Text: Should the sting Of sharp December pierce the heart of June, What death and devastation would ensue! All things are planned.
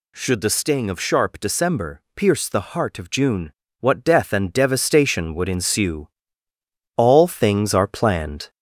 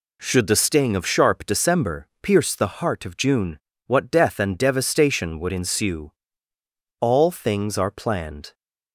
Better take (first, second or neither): second